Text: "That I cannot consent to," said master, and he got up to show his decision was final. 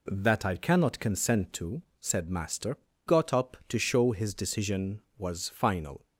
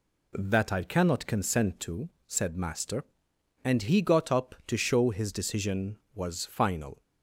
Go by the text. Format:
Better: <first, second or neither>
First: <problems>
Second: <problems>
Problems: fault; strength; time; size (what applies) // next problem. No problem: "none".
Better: second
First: skips "and he"; at 2.9 s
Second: none